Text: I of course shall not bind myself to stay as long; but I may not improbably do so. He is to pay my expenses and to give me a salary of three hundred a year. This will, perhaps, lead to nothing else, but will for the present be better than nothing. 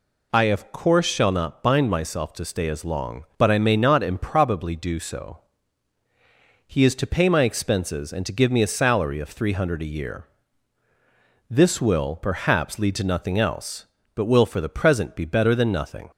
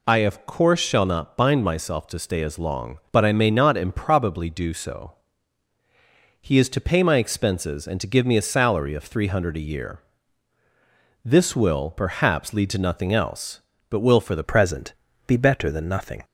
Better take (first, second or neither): first